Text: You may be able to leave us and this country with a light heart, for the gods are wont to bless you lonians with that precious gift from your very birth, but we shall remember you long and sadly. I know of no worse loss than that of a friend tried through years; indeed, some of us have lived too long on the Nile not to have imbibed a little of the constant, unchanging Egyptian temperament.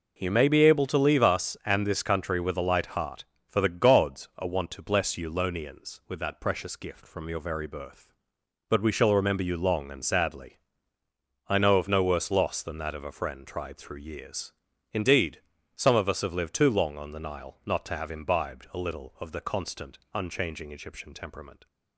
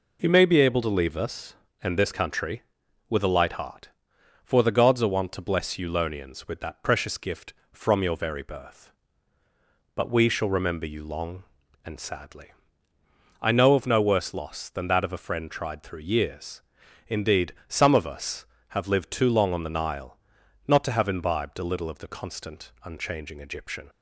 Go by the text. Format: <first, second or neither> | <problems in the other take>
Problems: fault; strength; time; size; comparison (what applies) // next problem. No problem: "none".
first | pauses between "Nile" and "not"; noticeable; at 20.1 s; 0.48 s long // stops before "temperament"; at 23.8 s